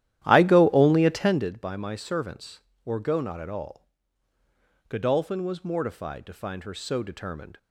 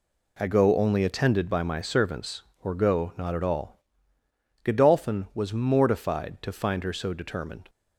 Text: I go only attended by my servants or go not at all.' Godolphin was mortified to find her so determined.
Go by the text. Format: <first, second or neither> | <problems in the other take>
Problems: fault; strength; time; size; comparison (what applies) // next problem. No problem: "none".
second | starts louder than the rest; strong; until 1.5 s; 12.5 dB